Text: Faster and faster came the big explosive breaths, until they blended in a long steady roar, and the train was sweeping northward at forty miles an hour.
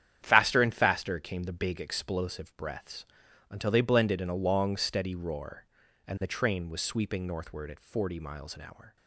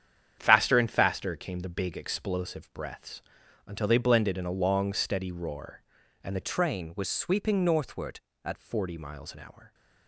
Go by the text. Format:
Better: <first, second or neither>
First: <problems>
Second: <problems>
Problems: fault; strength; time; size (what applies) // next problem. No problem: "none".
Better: first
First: starts louder than the rest; strong; until 1.2 s; 9.5 dB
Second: starts louder than the rest; strong; until 1.4 s; 8.5 dB // changes voice from "train" to "at"; from 6.4 to 8.5 s; 2.1 s long